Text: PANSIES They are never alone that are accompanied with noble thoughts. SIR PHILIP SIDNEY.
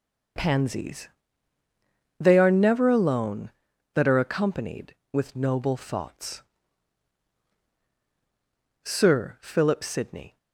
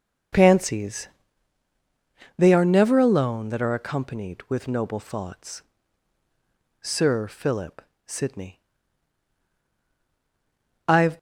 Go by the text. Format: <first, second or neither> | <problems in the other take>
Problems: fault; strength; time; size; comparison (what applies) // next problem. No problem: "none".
first | pauses between "PANSIES" and "They"; strong; at 1.0 s; 1.3 s long; also in the first // pauses between "PHILIP" and "SIDNEY"; slight; at 7.7 s; 0.28 s long // goes on to say "I'VE"; slight; from 10.8 s on; 0.30 s long